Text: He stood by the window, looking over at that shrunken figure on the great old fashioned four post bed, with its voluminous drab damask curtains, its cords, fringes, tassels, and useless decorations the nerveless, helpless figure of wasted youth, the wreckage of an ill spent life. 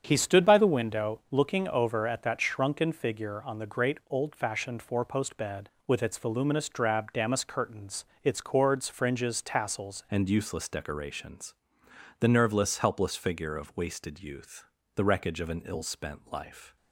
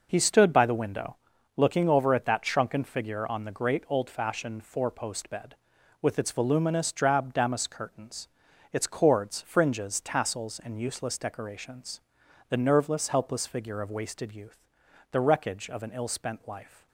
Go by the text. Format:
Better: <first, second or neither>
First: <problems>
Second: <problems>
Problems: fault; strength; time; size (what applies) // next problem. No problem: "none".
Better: second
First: starts louder than the rest; strong; until 1.0 s; 8 dB // changes voice at "and"; from 10.0 s on; 6.7 s long // pauses between "decorations" and "the"; noticeable; at 11.5 s; 0.66 s long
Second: pauses between "decorations" and "the"; noticeable; at 12.0 s; 0.48 s long